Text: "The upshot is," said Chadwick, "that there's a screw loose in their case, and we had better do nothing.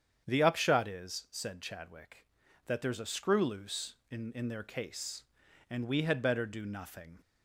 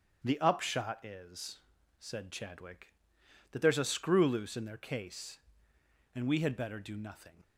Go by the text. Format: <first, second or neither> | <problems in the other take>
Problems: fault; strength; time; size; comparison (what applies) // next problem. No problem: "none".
second | starts louder than the rest; strong; until 1.3 s; 8 dB; strong in the second // says "in" twice; at 4.3 s